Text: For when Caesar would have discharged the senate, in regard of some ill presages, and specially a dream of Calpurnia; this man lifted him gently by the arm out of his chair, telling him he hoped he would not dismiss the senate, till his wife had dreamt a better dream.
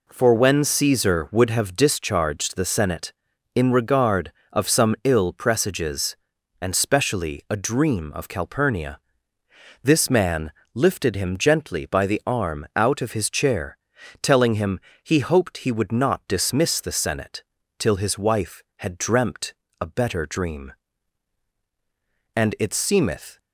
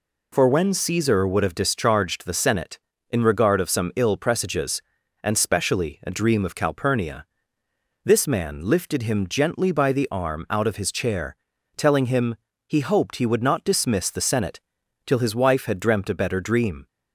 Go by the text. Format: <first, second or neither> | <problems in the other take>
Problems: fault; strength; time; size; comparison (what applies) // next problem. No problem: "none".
second | pauses between "man" and "lifted"; slight; at 10.4 s; 0.24 s long // pauses between "him" and "he"; slight; at 14.7 s; 0.24 s long; slight in the second // pauses between "dreamt" and "a"; slight; at 19.5 s; 0.26 s long // goes on to say "And it seemeth"; noticeable; from 22.3 s on; 1.0 s long